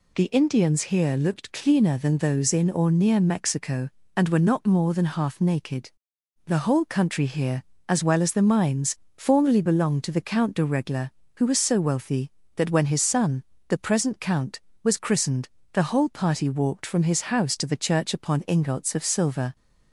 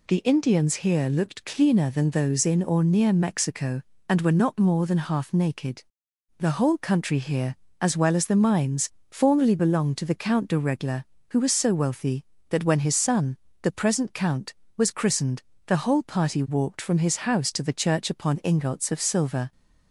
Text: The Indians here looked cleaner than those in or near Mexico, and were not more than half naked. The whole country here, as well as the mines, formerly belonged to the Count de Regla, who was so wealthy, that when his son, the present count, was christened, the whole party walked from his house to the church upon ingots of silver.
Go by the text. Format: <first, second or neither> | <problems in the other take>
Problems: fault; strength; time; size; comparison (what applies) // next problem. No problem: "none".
neither | none